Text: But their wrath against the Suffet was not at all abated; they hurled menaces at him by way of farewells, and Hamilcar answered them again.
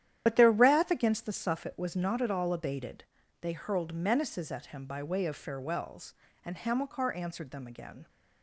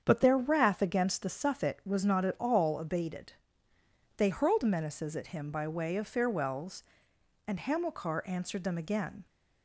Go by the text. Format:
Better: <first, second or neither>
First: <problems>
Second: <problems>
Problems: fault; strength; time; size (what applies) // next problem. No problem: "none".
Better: second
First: loses the start of "But"; at 0.2 s; 60 ms // starts louder than the rest; strong; until 1.2 s; 10.5 dB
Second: starts louder than the rest; strong; until 1.0 s; 7.5 dB